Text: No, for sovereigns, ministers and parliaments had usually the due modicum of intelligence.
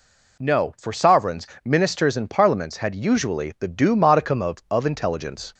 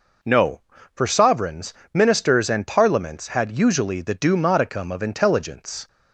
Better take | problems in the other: second | says "of" twice; at 4.6 s

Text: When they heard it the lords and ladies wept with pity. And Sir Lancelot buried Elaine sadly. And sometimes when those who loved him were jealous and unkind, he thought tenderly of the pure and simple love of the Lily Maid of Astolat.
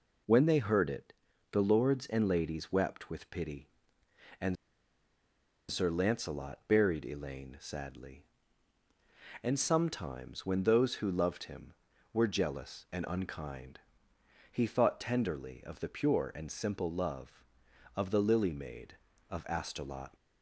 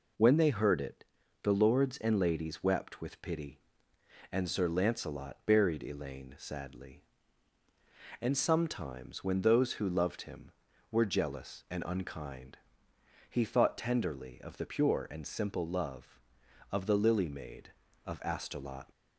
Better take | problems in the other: second | pauses between "it" and "the"; slight; at 1.1 s; 0.36 s long; slight in the second // pauses between "And" and "Sir"; at 4.5 s; 1.1 s long

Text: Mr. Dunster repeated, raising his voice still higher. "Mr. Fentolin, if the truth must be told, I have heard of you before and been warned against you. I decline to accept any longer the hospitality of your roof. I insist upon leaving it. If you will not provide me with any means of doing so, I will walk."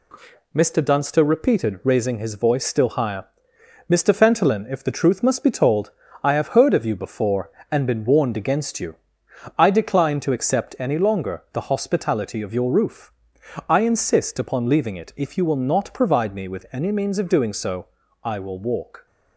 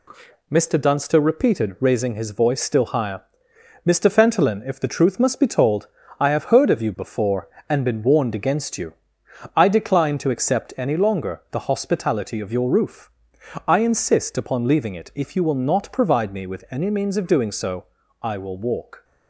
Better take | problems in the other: neither | none

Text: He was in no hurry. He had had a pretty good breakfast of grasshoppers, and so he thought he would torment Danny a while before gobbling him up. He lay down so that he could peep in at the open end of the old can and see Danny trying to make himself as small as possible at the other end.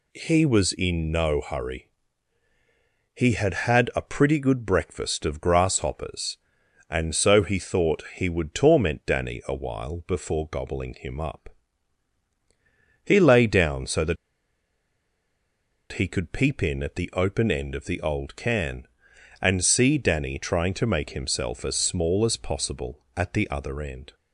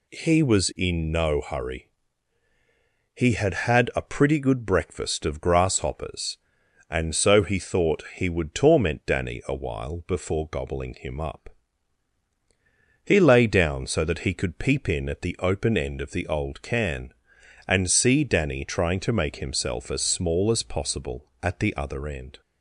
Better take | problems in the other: second | pauses between "that" and "he"; strong; at 14.1 s; 1.7 s long

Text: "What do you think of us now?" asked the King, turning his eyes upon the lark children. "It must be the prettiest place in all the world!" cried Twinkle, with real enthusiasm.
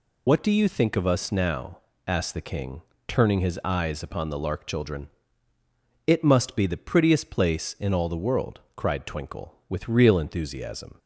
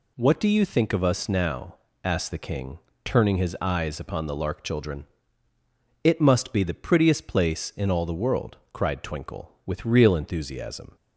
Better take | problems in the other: second | loses the start of "What"; at 0.2 s; 80 ms

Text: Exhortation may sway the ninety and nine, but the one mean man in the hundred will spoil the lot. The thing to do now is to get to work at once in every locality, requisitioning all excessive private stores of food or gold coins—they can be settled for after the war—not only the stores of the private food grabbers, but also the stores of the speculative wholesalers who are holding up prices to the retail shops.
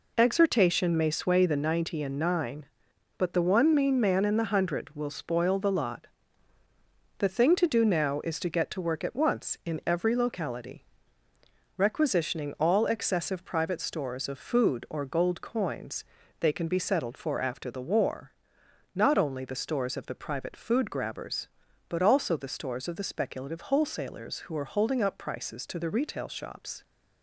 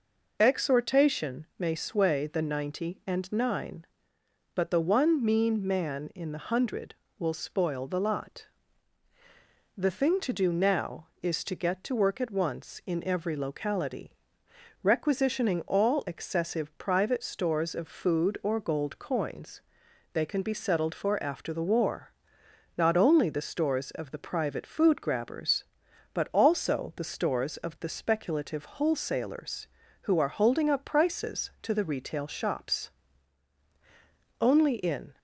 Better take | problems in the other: first | goes on to say "Only in"; noticeable; from 34.3 s on; 0.78 s long

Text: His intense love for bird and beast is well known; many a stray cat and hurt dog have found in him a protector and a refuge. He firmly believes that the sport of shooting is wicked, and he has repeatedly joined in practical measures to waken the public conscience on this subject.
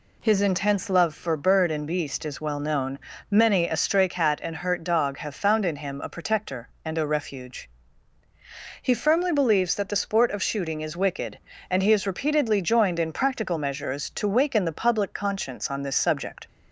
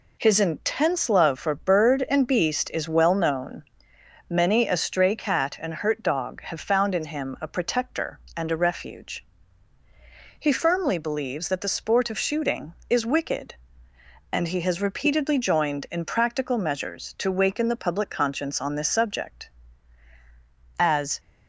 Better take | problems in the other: first | goes on to say "As"; slight; from 20.7 s on; 0.40 s long

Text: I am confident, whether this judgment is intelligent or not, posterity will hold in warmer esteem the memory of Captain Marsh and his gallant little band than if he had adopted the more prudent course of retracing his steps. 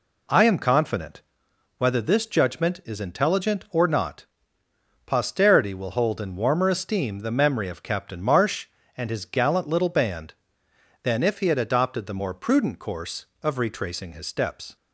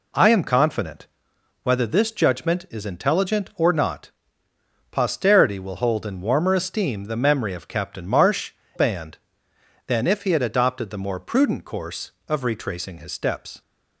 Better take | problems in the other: first | skips "and his gallant little"; at 8.6 s

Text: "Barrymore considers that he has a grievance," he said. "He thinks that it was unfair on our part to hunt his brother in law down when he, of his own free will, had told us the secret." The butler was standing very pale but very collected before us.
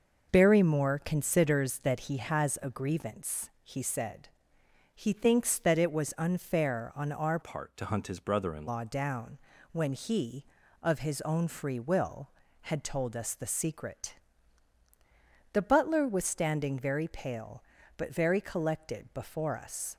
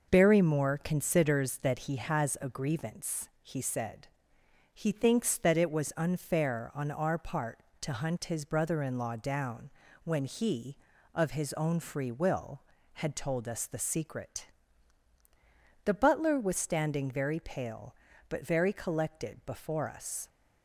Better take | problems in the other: second | changes voice from "part" to "in"; from 7.4 to 8.6 s; 1.2 s long // pauses between "down" and "when"; slight; at 9.3 s; 0.34 s long; slight in the second

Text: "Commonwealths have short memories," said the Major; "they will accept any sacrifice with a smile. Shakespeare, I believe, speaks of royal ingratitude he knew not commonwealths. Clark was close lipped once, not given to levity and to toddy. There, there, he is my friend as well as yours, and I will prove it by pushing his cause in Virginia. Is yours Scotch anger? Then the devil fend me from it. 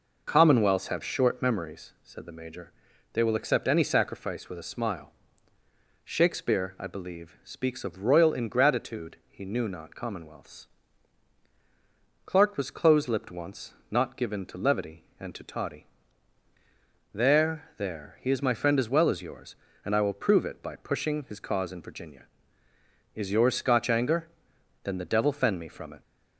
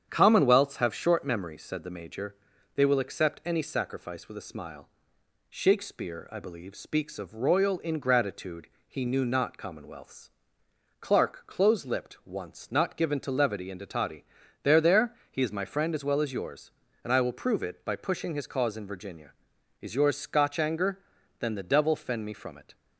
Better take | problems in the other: first | starts louder than the rest; strong; until 1.1 s; 8 dB // pauses between "ingratitude" and "he"; slight; at 8.6 s; 0.18 s long // skips "was"; at 11.4 s

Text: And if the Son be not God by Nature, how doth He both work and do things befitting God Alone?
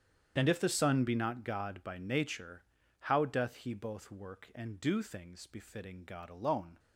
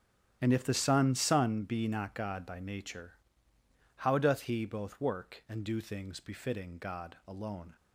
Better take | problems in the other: first | starts louder than the rest; strong; until 1.4 s; 10 dB; strong in the first // says "Son" twice; at 1.1 s

